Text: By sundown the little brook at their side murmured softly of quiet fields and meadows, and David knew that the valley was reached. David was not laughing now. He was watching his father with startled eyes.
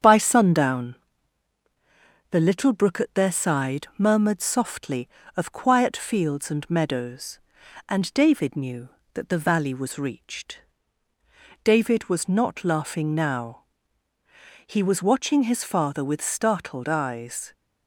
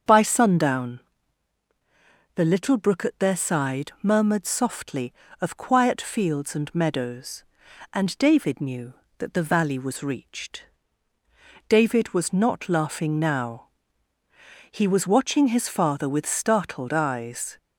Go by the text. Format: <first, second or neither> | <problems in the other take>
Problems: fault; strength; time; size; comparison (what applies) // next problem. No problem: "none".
second | gets quieter; slight; throughout; 2.5 dB // starts louder than the rest; strong; until 2.3 s; 8 dB; also in the second // pauses between "sundown" and "the"; strong; at 0.9 s; 1.3 s long; strong in the second